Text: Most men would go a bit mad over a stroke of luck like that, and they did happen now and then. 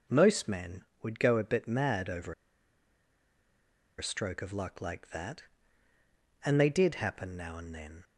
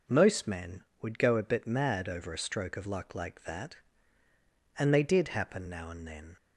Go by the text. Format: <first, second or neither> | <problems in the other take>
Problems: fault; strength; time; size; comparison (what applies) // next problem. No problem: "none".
second | pauses between "over" and "a"; strong; at 2.3 s; 1.6 s long